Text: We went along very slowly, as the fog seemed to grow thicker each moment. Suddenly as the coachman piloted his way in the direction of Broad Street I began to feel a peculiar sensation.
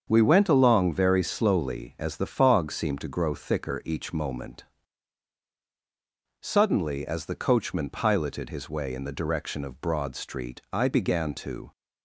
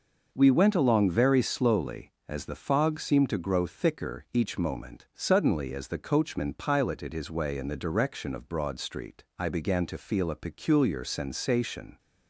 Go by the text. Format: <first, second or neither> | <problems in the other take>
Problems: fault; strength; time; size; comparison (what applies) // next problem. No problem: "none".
second | starts louder than the rest; until 1.1 s; 7 dB // stops before "feel a peculiar sensation"; at 11.7 s